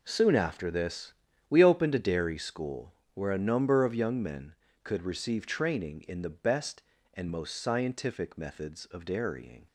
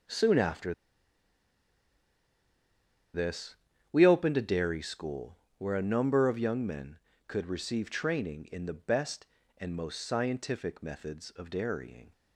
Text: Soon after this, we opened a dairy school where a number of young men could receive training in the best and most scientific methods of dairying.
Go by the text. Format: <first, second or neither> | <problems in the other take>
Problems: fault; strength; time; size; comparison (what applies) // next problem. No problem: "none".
first | pauses between "after" and "this"; strong; at 0.7 s; 2.4 s long // pauses between "school" and "where"; slight; at 5.3 s; 0.22 s long; slight in the first